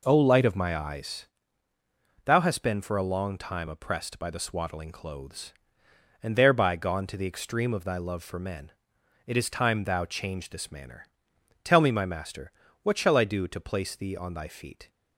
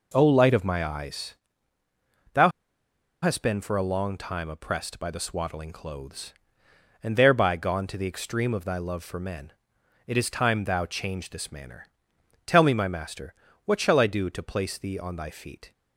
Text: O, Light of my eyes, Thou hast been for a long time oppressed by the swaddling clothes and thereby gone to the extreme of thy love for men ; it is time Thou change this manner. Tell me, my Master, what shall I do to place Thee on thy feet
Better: first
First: none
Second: pauses between "Thou" and "hast"; noticeable; at 2.5 s; 0.72 s long

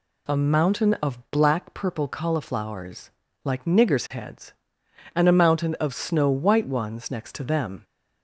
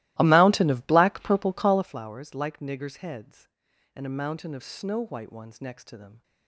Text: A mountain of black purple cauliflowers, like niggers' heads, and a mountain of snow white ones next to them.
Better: first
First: none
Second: starts louder than the rest; strong; until 2.0 s; 18 dB

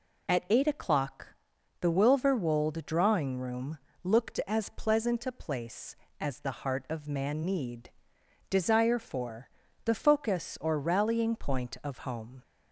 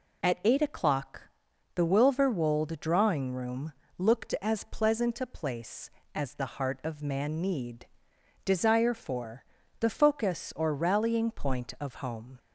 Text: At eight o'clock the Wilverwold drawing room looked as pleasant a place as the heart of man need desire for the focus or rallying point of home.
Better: neither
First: pauses between "o'clock" and "the"; noticeable; at 1.2 s; 0.52 s long // pauses between "room" and "looked"; slight; at 3.7 s; 0.28 s long // pauses between "need" and "desire"; noticeable; at 7.8 s; 0.62 s long // pauses between "for" and "the"; slight; at 9.4 s; 0.36 s long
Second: pauses between "o'clock" and "the"; noticeable; at 1.2 s; 0.52 s long // pauses between "room" and "looked"; slight; at 3.7 s; 0.28 s long // pauses between "need" and "desire"; noticeable; at 7.8 s; 0.60 s long // pauses between "for" and "the"; slight; at 9.4 s; 0.36 s long

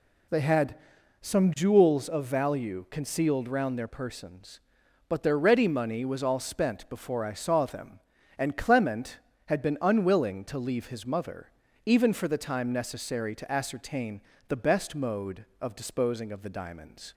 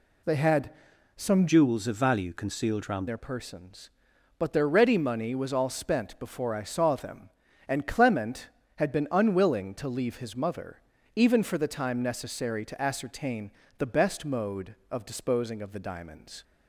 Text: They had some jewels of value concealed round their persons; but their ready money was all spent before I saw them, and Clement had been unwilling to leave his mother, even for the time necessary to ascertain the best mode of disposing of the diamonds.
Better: first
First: pauses between "had" and "some"; noticeable; at 0.7 s; 0.46 s long // pauses between "ascertain" and "the"; slight; at 14.2 s; 0.26 s long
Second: pauses between "had" and "some"; noticeable; at 0.7 s; 0.46 s long // changes voice from "jewels" to "round"; from 1.4 to 3.0 s; 1.6 s long // pauses between "ascertain" and "the"; slight; at 13.5 s; 0.26 s long

